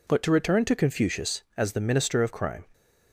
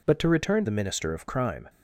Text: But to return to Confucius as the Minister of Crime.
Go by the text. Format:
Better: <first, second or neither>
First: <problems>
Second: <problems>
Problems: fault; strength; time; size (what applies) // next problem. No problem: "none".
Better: first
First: none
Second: skips "to Confucius as"; at 0.6 s